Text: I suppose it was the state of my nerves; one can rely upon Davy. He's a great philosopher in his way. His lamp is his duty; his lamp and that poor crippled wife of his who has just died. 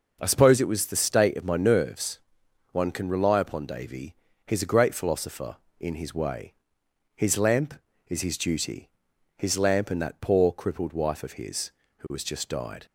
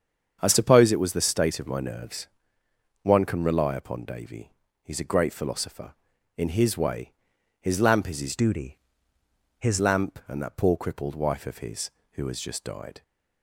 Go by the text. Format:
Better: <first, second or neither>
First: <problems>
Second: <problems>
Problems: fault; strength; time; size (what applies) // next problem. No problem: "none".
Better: first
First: none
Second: starts louder than the rest; strong; until 1.4 s; 7.5 dB // changes voice from "duty" to "his"; from 8.3 to 9.7 s; 1.4 s long